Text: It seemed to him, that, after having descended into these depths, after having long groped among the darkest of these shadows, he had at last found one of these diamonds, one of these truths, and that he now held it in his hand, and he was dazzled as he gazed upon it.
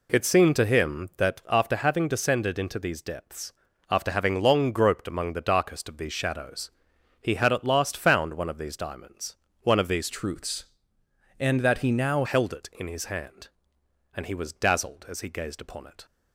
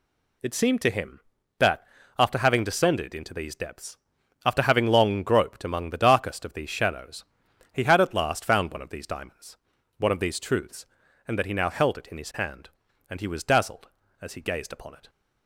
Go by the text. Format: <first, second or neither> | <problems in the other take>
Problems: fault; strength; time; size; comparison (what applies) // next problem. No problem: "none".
second | changes voice from "truths" to "now"; from 10.1 to 12.2 s; 2.1 s long